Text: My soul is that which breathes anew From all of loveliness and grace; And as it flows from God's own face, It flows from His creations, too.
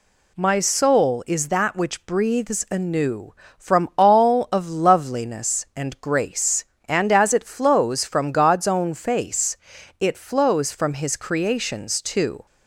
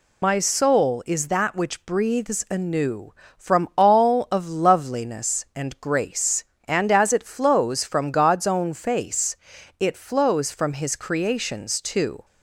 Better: first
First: none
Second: loses the start of "My"; at 0.2 s; 75 ms

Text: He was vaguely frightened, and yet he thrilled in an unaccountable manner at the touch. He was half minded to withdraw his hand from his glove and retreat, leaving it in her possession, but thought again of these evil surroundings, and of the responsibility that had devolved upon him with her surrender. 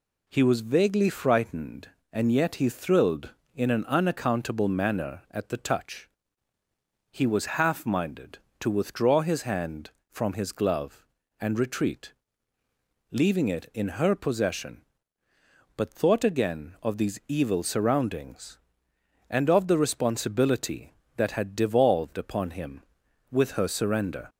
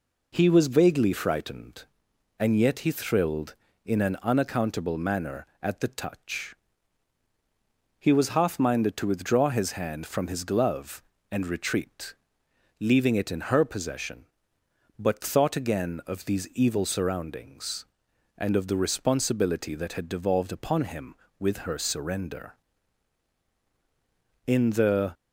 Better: first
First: none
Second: goes on to say "In the"; noticeable; from 24.4 s on; 0.66 s long

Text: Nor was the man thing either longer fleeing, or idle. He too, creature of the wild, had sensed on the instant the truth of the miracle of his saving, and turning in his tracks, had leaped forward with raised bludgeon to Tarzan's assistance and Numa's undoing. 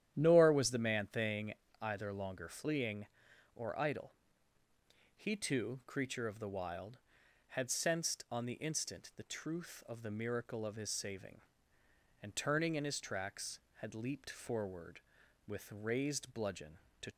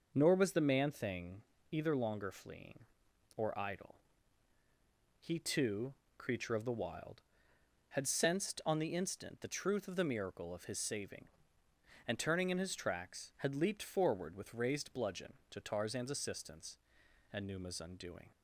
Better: second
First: starts louder than the rest; strong; until 1.1 s; 10.5 dB // pauses between "thing" and "either"; slight; at 1.5 s; 0.26 s long // stops before "Tarzan's assistance and Numa's undoing"; at 17.1 s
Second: pauses between "thing" and "either"; slight; at 1.4 s; 0.30 s long

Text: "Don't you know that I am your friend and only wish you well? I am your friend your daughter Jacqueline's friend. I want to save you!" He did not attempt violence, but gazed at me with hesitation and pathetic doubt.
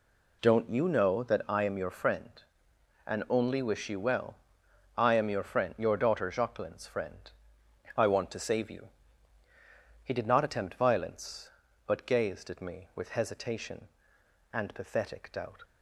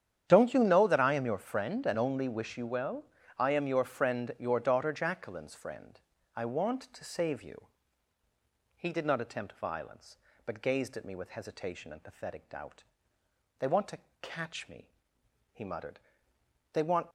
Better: first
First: none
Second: starts louder than the rest; strong; until 1.2 s; 9.5 dB // goes on to say "They want to catch me he muttered They want"; strong; from 13.5 s on; 3.5 s long

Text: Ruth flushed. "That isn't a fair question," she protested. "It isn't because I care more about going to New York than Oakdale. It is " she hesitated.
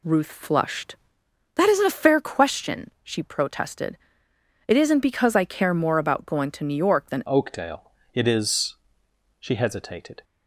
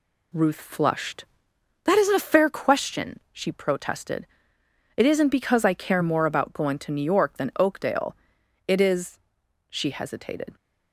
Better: second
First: changes voice at "Oakdale"; from 7.2 s on; 3.0 s long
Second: none

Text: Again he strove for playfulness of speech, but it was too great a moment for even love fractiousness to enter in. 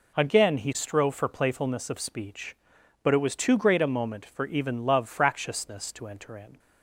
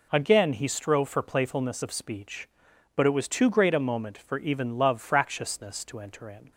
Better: neither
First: none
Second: none

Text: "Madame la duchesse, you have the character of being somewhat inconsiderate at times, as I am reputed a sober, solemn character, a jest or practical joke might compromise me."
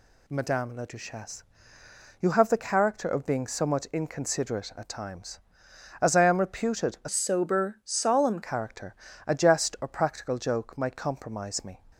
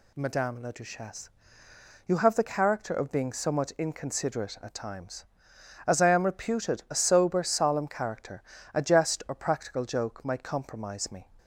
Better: second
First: changes voice from "sober" to "solemn"; from 7.0 to 8.3 s; 1.3 s long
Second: none

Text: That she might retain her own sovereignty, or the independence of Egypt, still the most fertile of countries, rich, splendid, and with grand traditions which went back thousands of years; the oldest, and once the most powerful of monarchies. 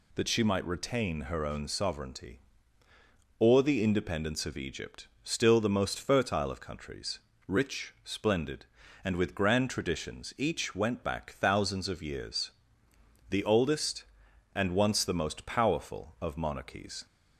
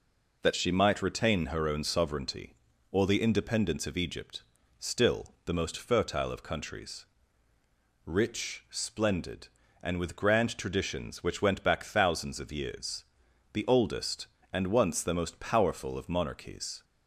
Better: second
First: says "each" for "which"; at 10.3 s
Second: none

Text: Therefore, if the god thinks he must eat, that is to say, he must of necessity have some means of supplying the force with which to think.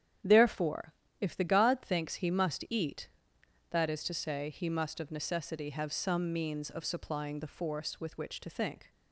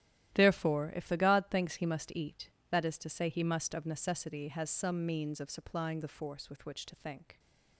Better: first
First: starts louder than the rest; strong; until 1.5 s; 9 dB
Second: starts louder than the rest; strong; until 1.3 s; 13 dB // says "has" for "have"; at 4.4 s

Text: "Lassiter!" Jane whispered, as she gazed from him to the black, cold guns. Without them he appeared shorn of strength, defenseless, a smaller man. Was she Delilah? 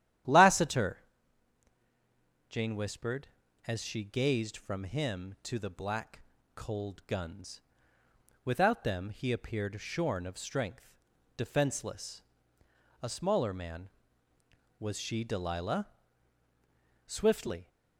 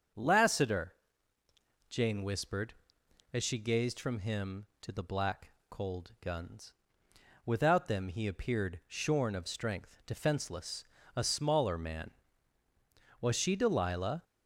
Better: second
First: starts louder than the rest; strong; until 2.7 s; 11 dB // goes on to say "Swiftly"; noticeable; from 17.0 s on; 0.62 s long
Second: starts louder than the rest; until 2.1 s; 7 dB

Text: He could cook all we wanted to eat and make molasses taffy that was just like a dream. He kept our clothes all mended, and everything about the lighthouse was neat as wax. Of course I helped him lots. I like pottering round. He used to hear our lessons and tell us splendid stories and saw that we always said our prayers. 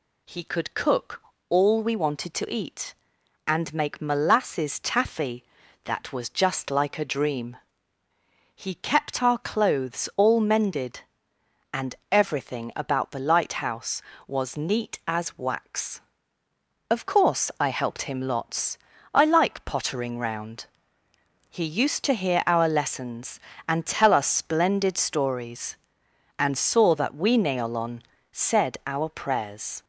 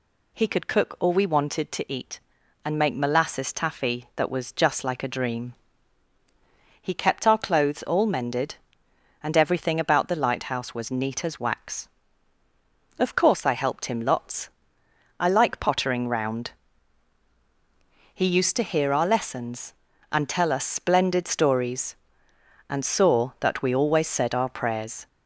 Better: second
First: pauses between "cook" and "all"; slight; at 1.2 s; 0.28 s long // pauses between "and" and "everything"; slight; at 11.9 s; 0.16 s long // says "neolon" for "always"; at 27.3 s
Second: none

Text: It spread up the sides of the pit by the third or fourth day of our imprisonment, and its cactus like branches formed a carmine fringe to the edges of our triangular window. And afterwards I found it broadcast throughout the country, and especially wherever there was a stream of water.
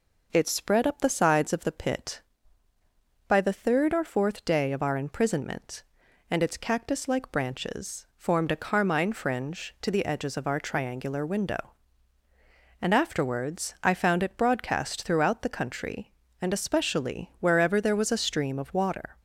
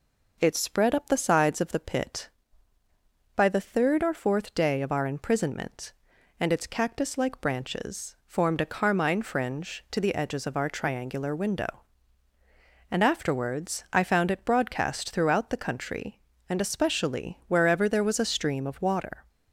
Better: neither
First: none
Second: none

